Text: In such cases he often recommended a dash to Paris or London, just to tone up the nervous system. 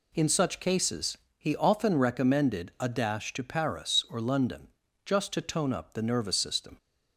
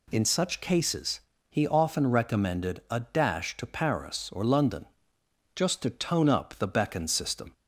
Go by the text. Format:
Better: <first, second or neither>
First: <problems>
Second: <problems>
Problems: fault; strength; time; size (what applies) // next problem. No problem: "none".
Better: first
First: pauses between "cases" and "he"; slight; at 1.1 s; 0.20 s long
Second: pauses between "cases" and "he"; slight; at 1.2 s; 0.30 s long // says "beckon" for "nervous"; at 6.6 s